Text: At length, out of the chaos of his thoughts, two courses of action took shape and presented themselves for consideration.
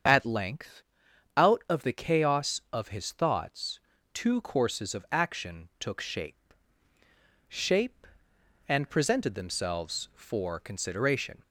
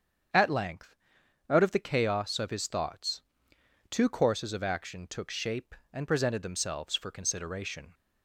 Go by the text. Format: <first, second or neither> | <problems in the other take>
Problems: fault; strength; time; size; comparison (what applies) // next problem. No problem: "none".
second | starts louder than the rest; strong; until 1.6 s; 7.5 dB; strong in the second // says "shape" twice; at 7.4 s